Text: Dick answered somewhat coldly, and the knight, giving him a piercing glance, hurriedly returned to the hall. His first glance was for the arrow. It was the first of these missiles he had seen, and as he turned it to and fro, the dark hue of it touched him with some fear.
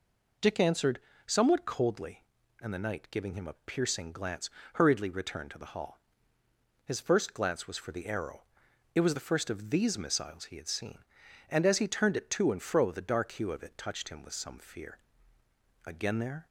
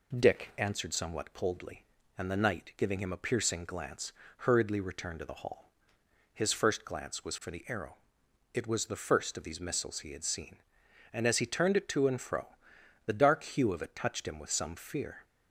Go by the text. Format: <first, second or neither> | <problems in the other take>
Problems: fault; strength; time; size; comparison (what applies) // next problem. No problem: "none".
second | pauses between "answered" and "somewhat"; slight; at 0.9 s; 0.26 s long // goes on to say "Again there"; noticeable; from 15.8 s on; 0.62 s long